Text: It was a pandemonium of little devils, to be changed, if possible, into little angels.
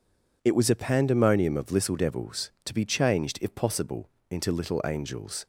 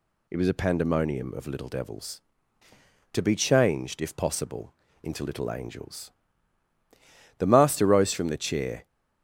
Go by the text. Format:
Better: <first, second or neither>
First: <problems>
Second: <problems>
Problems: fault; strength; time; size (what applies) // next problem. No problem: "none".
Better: first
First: none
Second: goes on to say "The master rose from the chair"; from 7.3 s on; 1.4 s long